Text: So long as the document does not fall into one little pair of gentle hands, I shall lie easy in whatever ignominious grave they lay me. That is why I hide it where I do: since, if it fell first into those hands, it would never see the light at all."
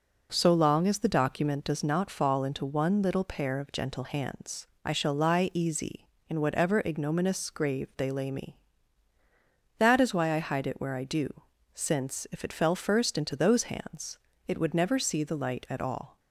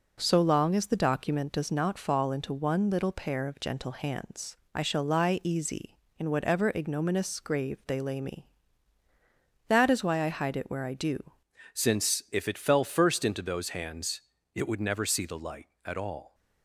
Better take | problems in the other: first | changes voice at "since"; from 11.7 s on; 4.6 s long

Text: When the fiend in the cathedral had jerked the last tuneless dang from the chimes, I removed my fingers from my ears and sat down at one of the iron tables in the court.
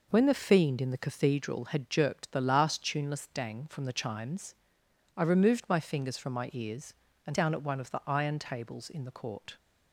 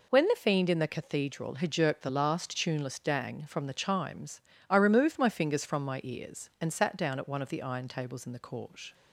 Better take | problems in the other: second | skips "sat"; at 7.3 s

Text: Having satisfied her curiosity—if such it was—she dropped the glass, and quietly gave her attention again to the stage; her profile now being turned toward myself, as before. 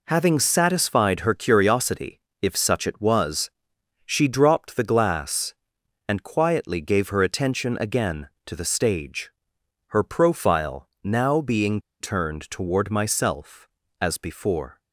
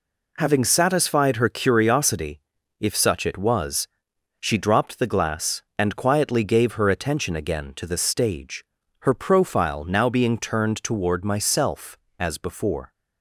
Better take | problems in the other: second | pauses between "profile" and "now"; slight; at 10.8 s; 0.16 s long // pauses between "being" and "turned"; slight; at 11.7 s; 0.21 s long

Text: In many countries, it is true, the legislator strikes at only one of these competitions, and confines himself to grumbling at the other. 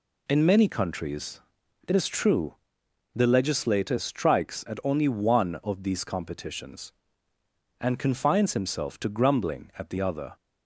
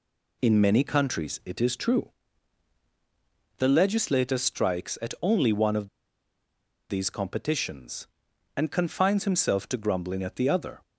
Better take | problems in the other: first | pauses between "of" and "these"; at 5.8 s; 1.0 s long

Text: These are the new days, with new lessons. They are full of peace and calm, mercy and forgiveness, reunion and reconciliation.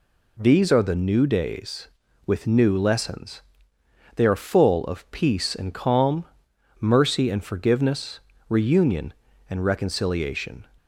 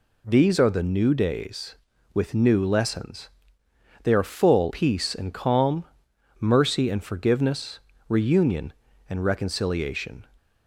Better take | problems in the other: first | skips "of"; at 4.7 s

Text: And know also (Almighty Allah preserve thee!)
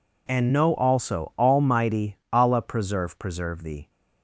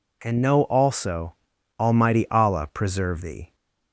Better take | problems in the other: second | says "preserve" twice; at 3.1 s

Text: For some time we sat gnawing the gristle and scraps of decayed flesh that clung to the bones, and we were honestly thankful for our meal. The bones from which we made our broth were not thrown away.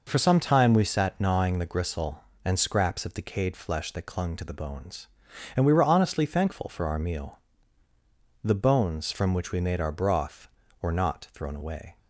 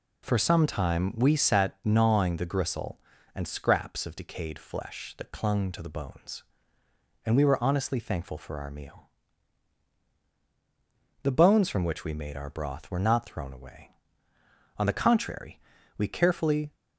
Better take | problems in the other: first | goes on to say "On the contrary we carefully"; strong; from 14.7 s on; 1.9 s long

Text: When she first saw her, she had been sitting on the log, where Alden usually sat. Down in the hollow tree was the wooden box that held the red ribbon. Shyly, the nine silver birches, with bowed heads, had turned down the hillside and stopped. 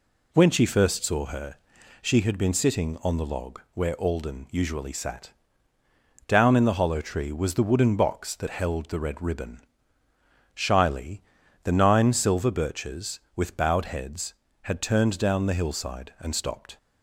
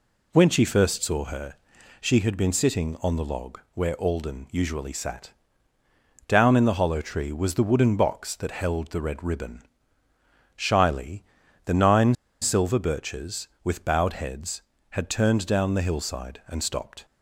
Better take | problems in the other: first | pauses between "nine" and "silver"; slight; at 12.1 s; 0.28 s long

